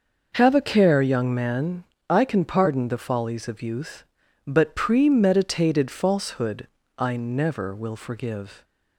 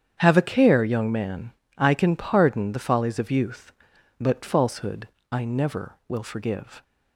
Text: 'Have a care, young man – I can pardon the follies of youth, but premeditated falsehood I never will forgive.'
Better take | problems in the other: first | starts louder than the rest; strong; until 1.2 s; 8.5 dB // skips "premeditated"; at 4.4 s // pauses between "falsehood" and "I"; slight; at 5.0 s; 0.22 s long; slight in the first

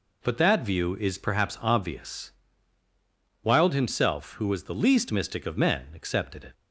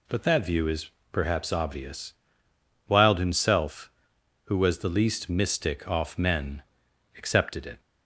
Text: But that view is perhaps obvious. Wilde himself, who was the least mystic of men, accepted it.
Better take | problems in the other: first | pauses between "is" and "perhaps"; slight; at 0.8 s; 0.22 s long // says "off" for "of"; at 5.8 s

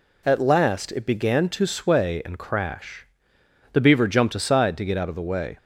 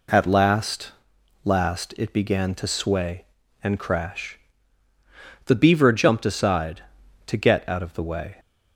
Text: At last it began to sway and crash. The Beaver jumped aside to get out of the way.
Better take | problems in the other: first | says "last" twice; at 1.4 s

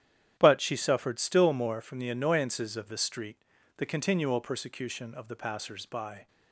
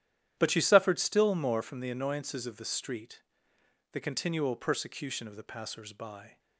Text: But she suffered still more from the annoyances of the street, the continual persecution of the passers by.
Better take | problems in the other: neither | starts louder than the rest; strong; the same in both

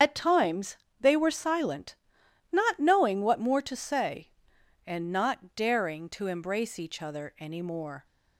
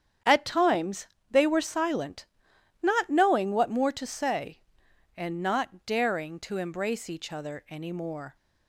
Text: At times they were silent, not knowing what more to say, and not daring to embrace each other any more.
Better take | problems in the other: second | loses the start of "At"; at 0.0 s; 75 ms // starts louder than the rest; strong; until 1.2 s; 7.5 dB; strong in the second // pauses between "times" and "they"; slight; at 0.7 s; 0.24 s long; slight in the second

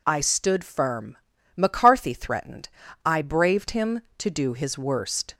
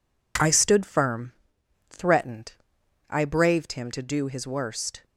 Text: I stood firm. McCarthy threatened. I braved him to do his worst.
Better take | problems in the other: first | skips "McCarthy"; at 1.5 s

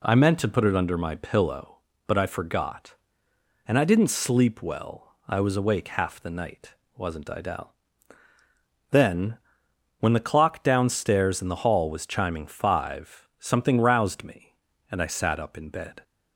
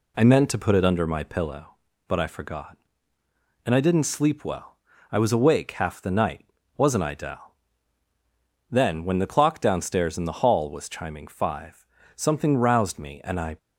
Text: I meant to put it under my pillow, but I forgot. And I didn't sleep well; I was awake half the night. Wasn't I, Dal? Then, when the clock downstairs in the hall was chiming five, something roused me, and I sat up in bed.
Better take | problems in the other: first | stops before "sat up in bed"; at 13.5 s

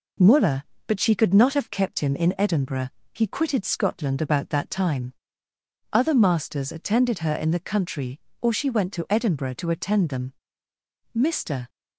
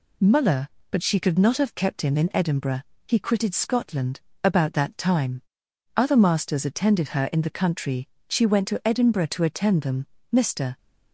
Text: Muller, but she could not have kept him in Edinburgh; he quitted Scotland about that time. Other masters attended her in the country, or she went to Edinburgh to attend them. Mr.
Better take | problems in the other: first | pauses between "Scotland" and "about"; slight; at 4.1 s; 0.24 s long // skips "or"; at 8.1 s

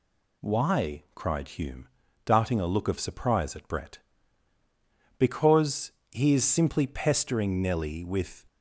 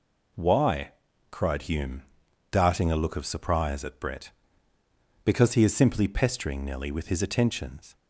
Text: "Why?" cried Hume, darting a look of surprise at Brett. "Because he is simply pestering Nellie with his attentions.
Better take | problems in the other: second | pauses between "Because" and "he"; slight; at 5.9 s; 0.20 s long // stops before "his attentions"; at 8.4 s

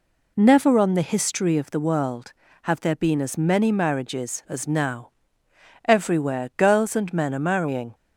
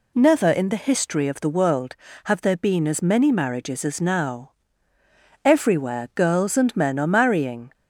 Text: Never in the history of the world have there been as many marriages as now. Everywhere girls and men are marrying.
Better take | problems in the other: second | says "on" for "in"; at 0.7 s

